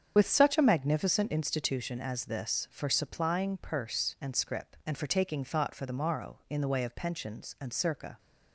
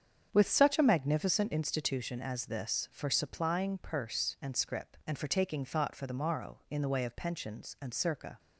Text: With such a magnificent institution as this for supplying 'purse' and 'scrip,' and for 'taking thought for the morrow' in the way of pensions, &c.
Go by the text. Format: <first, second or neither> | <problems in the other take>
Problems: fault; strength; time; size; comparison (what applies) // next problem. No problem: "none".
second | loses the start of "With"; at 0.1 s; 45 ms // starts louder than the rest; strong; until 1.1 s; 7.5 dB; strong in the second